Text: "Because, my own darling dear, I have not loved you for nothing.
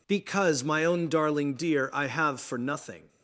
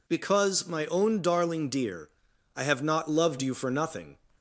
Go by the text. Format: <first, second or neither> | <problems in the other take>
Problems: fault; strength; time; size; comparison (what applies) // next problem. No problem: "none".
second | skips "not loved you"; at 2.3 s